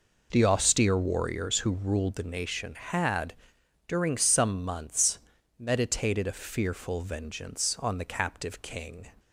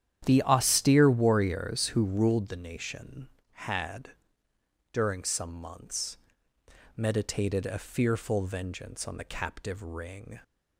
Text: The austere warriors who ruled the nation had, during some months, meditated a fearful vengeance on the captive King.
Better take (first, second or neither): first